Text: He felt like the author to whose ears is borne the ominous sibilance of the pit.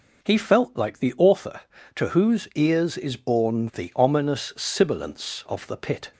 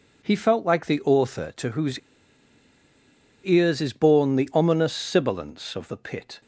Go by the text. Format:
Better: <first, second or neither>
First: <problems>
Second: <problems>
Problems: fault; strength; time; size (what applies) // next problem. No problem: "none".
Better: first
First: none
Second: pauses between "whose" and "ears"; strong; at 1.9 s; 1.4 s long